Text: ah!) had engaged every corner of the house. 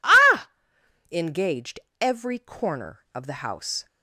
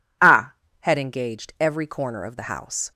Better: second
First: skips "had"; at 0.7 s // pauses between "engaged" and "every"; slight; at 1.8 s; 0.22 s long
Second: none

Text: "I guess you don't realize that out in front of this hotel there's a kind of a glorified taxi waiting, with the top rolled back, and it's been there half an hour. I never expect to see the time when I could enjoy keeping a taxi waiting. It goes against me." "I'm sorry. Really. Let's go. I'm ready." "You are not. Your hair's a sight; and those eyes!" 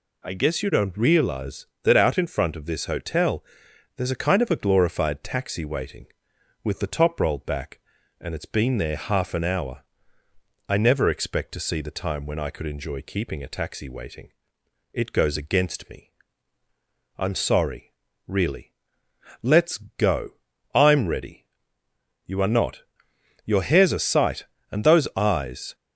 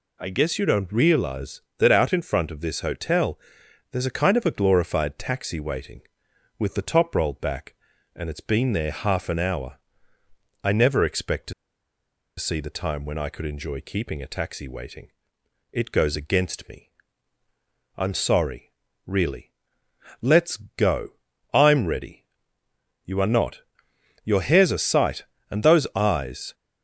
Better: first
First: pauses between "hotel" and "there's"; noticeable; at 3.4 s; 0.54 s long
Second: pauses between "hotel" and "there's"; noticeable; at 3.3 s; 0.54 s long // pauses between "to" and "see"; noticeable; at 11.5 s; 0.84 s long

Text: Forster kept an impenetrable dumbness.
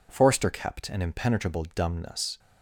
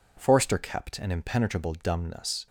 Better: neither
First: none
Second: none

